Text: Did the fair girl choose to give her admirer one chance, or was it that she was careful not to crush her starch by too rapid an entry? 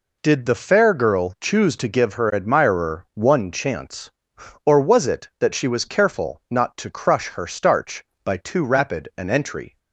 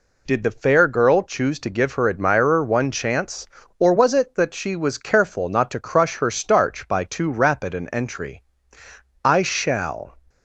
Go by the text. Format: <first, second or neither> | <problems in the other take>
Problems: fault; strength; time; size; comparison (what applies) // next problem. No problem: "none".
first | goes on to say "I shall"; noticeable; from 9.2 s on; 0.94 s long